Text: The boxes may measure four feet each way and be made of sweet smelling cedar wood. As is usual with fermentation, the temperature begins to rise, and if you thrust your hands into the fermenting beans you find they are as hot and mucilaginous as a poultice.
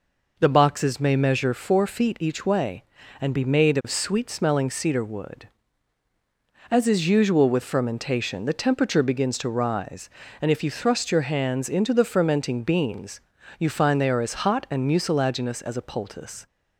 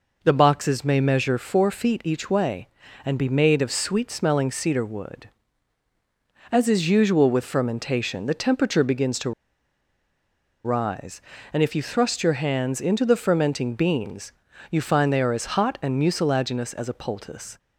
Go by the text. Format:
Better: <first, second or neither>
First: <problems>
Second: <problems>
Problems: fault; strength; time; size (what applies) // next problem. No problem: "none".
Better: first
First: pauses between "beans" and "you"; at 13.2 s; 0.38 s long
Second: pauses between "to" and "rise"; strong; at 9.3 s; 1.3 s long // pauses between "beans" and "you"; at 14.3 s; 0.38 s long